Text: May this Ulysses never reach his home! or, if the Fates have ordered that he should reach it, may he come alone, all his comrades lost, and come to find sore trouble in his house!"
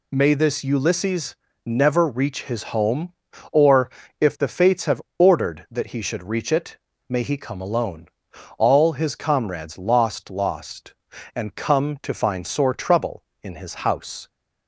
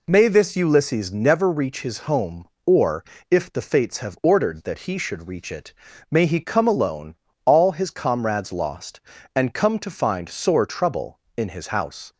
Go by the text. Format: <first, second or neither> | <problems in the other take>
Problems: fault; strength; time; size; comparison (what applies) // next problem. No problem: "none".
second | pauses between "Ulysses" and "never"; slight; at 1.3 s; 0.32 s long // pauses between "have" and "ordered"; slight; at 5.0 s; 0.16 s long // says "lost" twice; at 10.2 s